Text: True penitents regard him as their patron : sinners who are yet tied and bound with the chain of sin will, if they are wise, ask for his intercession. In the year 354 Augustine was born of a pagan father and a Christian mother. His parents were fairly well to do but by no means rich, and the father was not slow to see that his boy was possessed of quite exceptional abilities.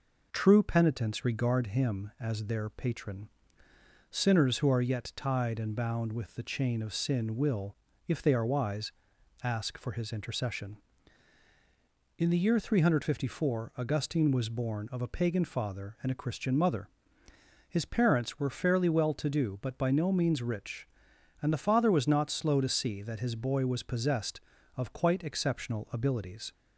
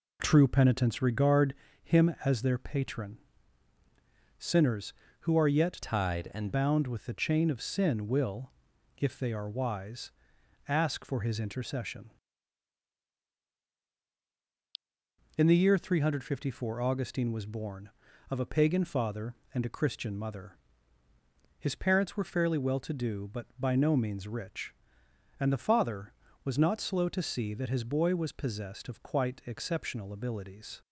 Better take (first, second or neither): first